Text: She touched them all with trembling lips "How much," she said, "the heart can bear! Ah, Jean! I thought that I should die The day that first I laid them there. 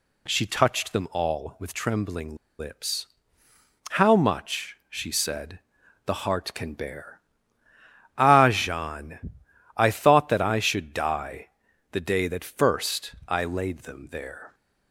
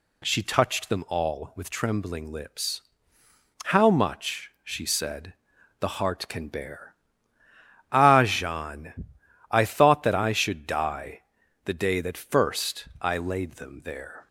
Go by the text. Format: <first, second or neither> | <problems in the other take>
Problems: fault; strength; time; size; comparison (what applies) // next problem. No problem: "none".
second | pauses between "trembling" and "lips"; slight; at 2.3 s; 0.24 s long // pauses between "lips" and "How"; noticeable; at 3.0 s; 0.86 s long; noticeable in the second // pauses between "die" and "The"; at 11.5 s; 0.40 s long; also in the second